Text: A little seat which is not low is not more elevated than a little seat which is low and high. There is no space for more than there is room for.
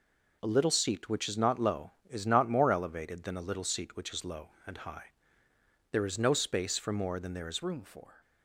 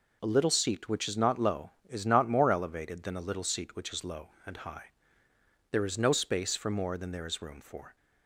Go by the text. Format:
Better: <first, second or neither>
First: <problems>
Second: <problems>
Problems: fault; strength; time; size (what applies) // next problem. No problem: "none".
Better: second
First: changes voice at "room"; from 7.6 s on; 0.5 s long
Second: none